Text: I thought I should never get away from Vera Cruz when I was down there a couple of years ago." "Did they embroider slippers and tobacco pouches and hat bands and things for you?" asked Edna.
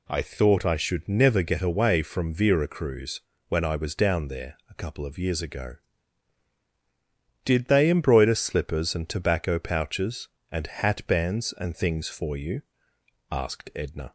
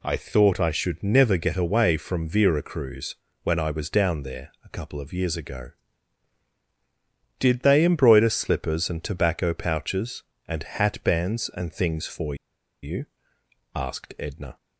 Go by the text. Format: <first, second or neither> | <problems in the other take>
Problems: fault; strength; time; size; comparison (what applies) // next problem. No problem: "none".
first | pauses between "Cruz" and "when"; slight; at 3.1 s; 0.28 s long; slight in the first // pauses between "for" and "you"; noticeable; at 12.3 s; 0.47 s long